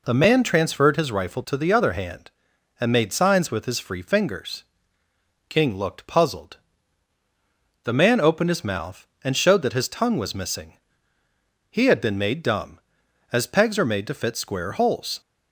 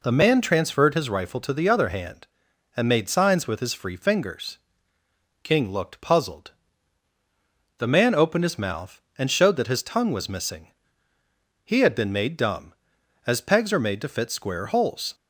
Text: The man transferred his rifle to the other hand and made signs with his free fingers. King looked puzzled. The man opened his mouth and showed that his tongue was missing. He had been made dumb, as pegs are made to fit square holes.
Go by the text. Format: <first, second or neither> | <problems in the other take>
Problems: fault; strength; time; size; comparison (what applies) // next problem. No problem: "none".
neither | none